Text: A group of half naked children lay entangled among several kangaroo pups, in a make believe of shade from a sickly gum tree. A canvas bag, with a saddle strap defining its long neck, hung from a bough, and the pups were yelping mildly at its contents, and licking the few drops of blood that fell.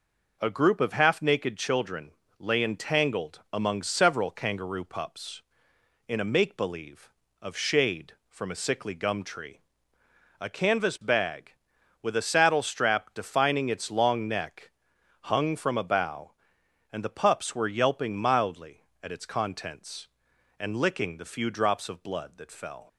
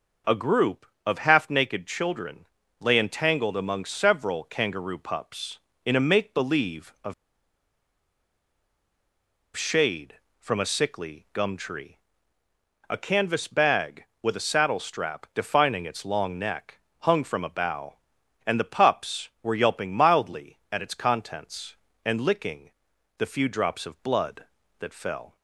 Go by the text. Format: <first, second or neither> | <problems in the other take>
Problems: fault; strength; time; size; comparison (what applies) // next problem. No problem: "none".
first | pauses between "children" and "lay"; slight; at 2.4 s; 0.36 s long; slight in the first // pauses between "of" and "shade"; strong; at 7.1 s; 2.4 s long // pauses between "licking" and "the"; noticeable; at 22.7 s; 0.48 s long